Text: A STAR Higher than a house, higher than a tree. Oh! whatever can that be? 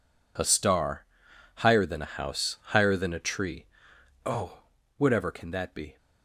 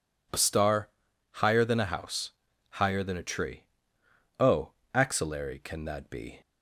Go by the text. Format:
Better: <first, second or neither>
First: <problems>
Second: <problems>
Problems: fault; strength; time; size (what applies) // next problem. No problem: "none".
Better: first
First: pauses between "STAR" and "Higher"; noticeable; at 1.0 s; 0.54 s long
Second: pauses between "STAR" and "Higher"; at 0.8 s; 0.44 s long // says "axillary" for "whatever"; at 4.9 s